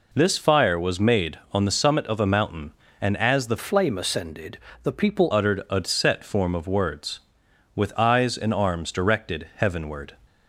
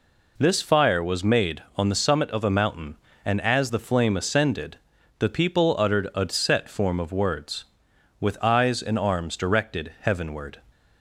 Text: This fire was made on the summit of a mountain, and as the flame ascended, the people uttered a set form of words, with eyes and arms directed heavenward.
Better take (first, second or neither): second